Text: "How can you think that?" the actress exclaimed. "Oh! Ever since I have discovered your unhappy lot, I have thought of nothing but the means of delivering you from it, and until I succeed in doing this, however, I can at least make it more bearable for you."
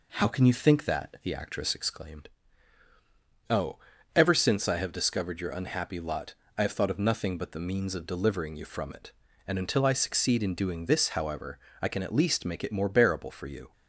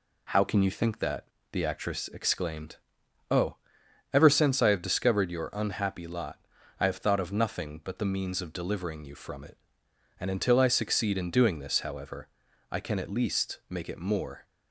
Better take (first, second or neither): first